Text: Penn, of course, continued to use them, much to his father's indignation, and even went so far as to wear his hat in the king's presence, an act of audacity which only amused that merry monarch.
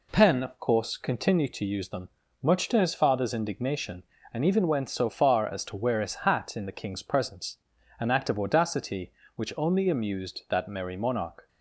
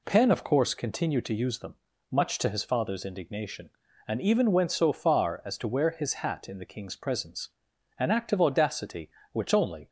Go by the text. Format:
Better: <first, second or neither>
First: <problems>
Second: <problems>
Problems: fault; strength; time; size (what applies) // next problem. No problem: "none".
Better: first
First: none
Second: stops before "amused that merry monarch"; at 9.8 s